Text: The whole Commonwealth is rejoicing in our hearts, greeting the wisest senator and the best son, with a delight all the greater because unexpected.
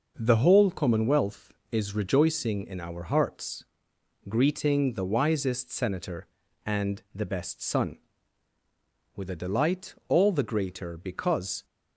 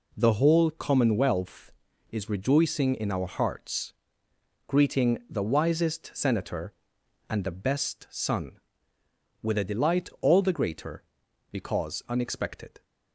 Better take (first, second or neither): second